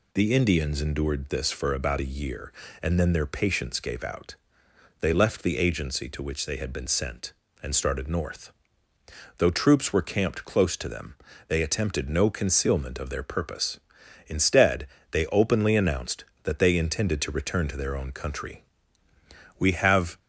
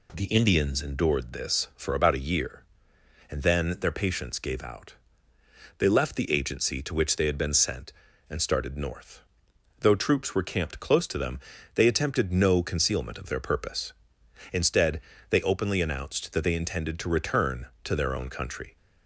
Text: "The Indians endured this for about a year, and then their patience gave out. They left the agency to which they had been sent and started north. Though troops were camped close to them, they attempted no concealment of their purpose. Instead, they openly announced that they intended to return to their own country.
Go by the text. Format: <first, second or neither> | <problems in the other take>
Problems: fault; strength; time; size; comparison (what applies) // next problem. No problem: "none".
second | goes on to say "We have"; noticeable; from 19.5 s on; 0.62 s long